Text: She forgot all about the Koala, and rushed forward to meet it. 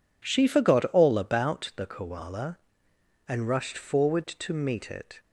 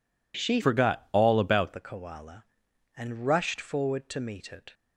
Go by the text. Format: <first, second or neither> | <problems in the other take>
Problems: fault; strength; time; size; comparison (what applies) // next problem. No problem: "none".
first | changes voice from "forgot" to "about"; from 0.6 to 1.7 s; 1.1 s long